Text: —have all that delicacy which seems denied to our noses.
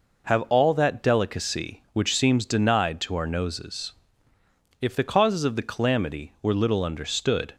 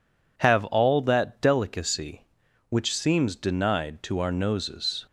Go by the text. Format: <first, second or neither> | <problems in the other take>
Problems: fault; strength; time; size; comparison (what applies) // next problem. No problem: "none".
second | goes on to say "If the causes of the calamity were little understood"; strong; from 4.8 s on; 2.7 s long